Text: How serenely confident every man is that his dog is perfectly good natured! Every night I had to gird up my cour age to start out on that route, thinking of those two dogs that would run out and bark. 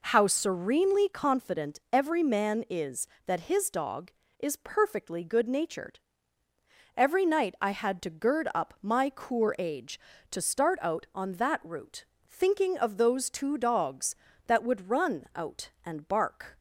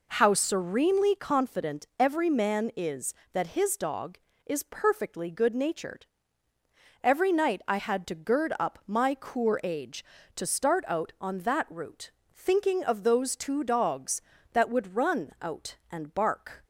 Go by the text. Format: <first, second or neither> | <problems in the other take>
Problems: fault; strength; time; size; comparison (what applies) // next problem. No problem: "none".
neither | none